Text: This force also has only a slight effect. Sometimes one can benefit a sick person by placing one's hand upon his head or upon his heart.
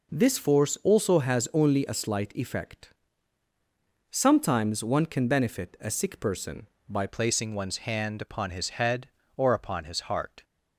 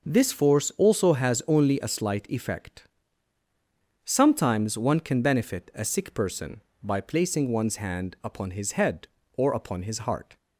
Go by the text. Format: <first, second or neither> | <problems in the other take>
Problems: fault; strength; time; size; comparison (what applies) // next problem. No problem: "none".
second | changes voice at "placing"; from 7.0 s on; 3.4 s long